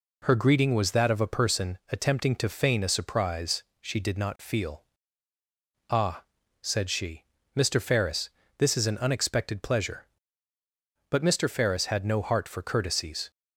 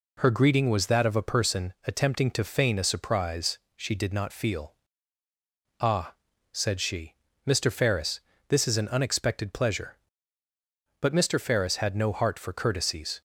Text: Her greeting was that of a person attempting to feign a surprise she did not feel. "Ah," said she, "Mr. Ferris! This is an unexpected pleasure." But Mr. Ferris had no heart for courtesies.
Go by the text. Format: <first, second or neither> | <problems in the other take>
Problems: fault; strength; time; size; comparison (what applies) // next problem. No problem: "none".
neither | pauses between "surprise" and "she"; slight; the same in both